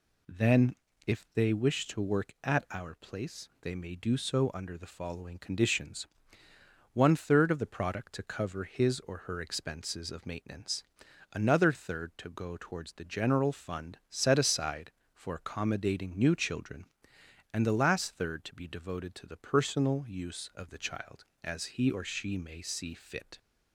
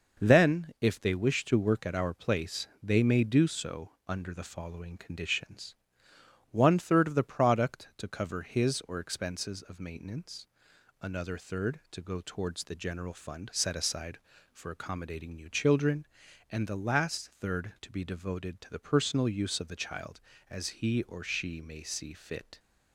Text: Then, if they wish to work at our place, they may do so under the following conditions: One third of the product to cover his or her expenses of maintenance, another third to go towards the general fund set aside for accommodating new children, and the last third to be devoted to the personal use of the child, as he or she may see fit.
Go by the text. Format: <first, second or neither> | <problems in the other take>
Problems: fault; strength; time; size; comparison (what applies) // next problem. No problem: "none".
first | pauses between "so" and "under"; slight; at 3.8 s; 0.18 s long // skips "her"; at 8.9 s